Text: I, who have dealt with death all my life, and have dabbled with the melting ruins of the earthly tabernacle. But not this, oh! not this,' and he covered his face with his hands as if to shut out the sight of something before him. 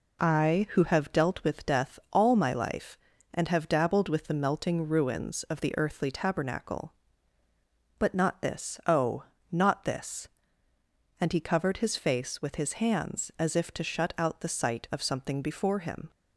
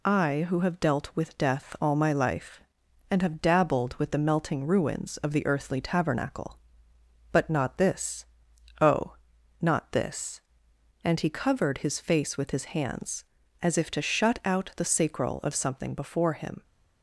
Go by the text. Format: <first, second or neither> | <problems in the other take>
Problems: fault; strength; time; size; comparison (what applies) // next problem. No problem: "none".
first | says "sacral" for "sight"; at 14.8 s